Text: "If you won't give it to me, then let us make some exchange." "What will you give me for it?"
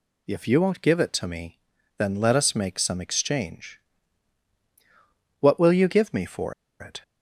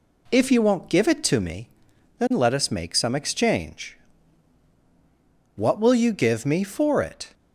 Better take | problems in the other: second | pauses between "for" and "it"; slight; at 6.5 s; 0.26 s long

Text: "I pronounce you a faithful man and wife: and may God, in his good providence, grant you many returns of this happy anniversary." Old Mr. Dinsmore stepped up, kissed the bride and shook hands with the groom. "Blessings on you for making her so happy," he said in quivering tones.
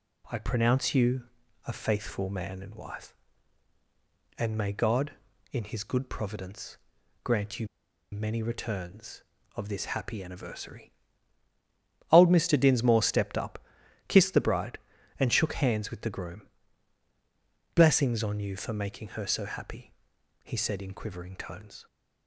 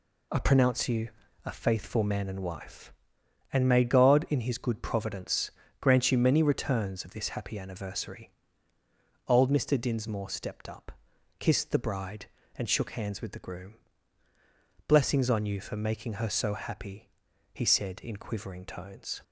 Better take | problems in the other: second | pauses between "you" and "a"; at 1.2 s; 0.42 s long; slight in the second // pauses between "you" and "many"; at 7.6 s; 0.44 s long

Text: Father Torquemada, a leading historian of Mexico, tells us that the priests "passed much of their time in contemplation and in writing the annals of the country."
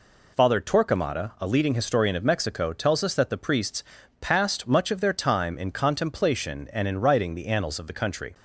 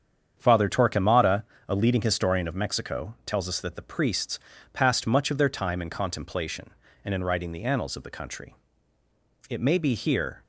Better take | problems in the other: first | starts louder than the rest; strong; until 1.3 s; 8 dB // pauses between "priests" and "passed"; slight; at 4.3 s; 0.34 s long; slight in the first // goes on to say "It may be here"; noticeable; from 9.4 s on; 0.92 s long

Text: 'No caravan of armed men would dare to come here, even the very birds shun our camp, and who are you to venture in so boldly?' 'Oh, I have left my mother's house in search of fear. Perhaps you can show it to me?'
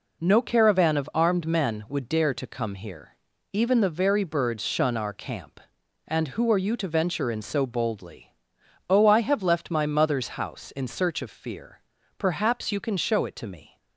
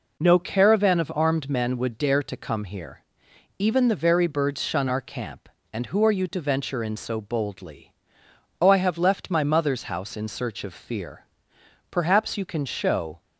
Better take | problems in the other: first | stops before "it to me"; at 13.2 s

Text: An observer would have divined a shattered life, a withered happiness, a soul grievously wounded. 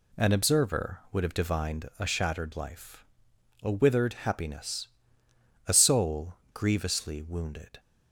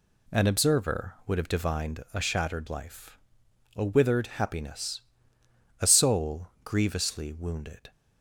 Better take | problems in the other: neither | pauses between "soul" and "grievously"; slight; the same in both

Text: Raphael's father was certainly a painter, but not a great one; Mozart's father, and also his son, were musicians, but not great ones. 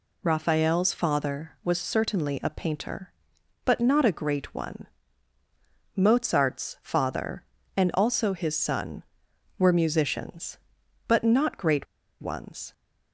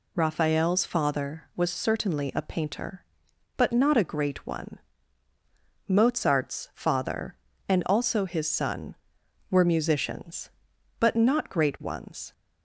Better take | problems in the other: second | pauses between "great" and "ones"; at 11.8 s; 0.37 s long

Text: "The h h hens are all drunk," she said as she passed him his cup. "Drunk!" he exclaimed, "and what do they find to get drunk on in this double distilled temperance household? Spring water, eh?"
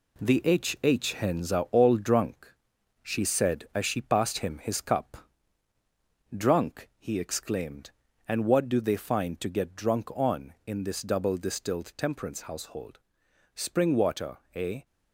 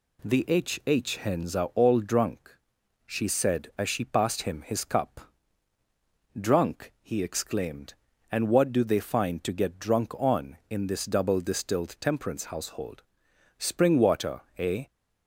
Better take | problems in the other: second | gets quieter; noticeable; throughout; 5.5 dB

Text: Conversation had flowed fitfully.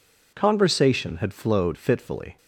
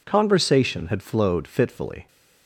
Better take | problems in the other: neither | none

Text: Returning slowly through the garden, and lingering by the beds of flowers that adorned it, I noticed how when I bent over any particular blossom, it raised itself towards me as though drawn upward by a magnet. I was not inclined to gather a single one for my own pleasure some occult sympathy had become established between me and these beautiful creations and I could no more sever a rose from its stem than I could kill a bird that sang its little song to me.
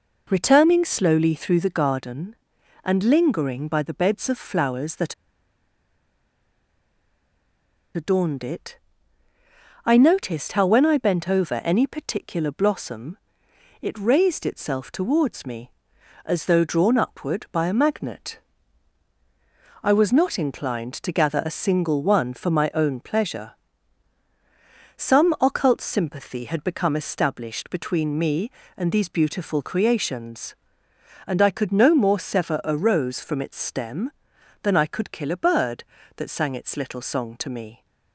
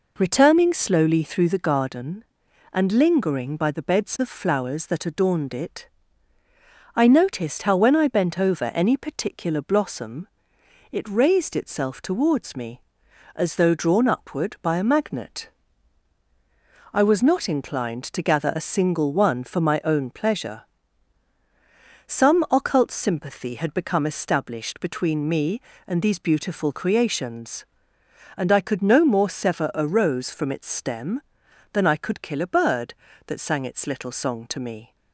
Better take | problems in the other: second | pauses between "that" and "adorned"; strong; at 5.1 s; 2.8 s long // pauses between "pleasure" and "some"; strong; at 23.5 s; 1.4 s long; strong in the second

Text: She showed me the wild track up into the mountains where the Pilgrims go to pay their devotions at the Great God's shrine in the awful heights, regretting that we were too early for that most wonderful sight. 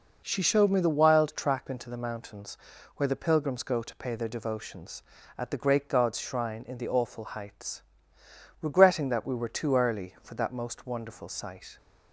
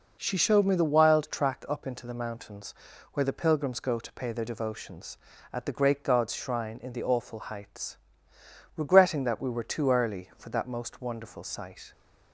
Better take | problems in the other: second | skips "up"; at 1.6 s // pauses between "mountains" and "where"; at 2.5 s; 0.40 s long; also in the second

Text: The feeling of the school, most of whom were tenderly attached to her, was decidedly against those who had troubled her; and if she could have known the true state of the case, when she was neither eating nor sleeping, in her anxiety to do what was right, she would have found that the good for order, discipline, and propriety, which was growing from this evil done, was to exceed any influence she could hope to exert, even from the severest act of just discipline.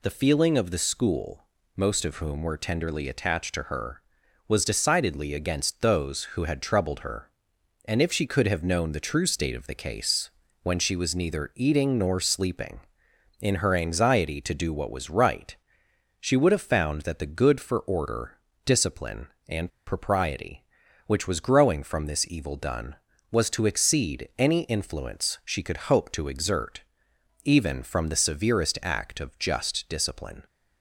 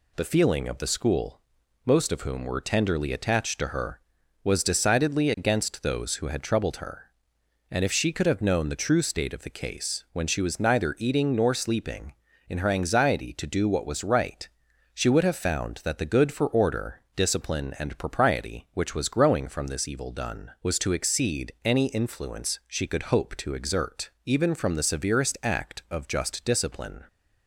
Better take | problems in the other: second | pauses between "and" and "propriety"; slight; at 19.6 s; 0.19 s long

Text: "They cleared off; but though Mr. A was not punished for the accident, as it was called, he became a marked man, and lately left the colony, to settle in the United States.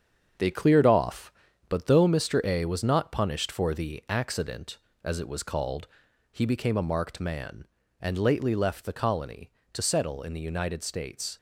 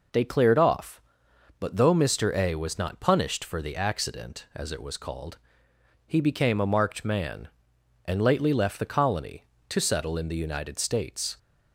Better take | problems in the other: second | gets quieter; throughout; 7 dB

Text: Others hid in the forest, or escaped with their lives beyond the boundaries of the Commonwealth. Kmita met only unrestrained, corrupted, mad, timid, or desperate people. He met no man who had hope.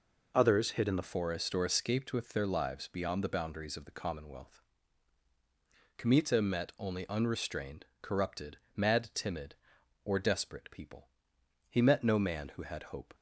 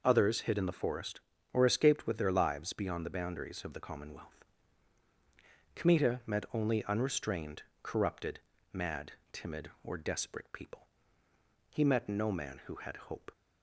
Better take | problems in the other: second | changes voice at "forest"; from 1.0 s on; 12.1 s long

